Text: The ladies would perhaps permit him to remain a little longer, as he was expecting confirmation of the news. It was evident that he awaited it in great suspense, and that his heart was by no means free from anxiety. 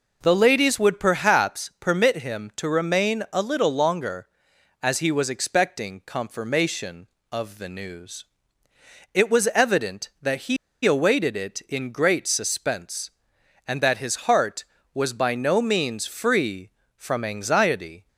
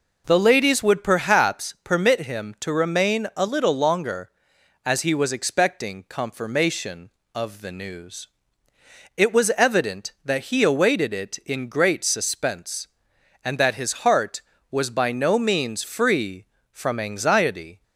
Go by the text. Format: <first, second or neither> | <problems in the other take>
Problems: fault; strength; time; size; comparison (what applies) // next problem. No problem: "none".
second | pauses between "he" and "awaited"; slight; at 10.5 s; 0.28 s long